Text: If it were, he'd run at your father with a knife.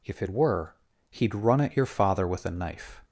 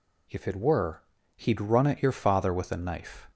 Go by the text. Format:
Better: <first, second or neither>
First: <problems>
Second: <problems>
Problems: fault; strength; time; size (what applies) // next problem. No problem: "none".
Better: neither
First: none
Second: none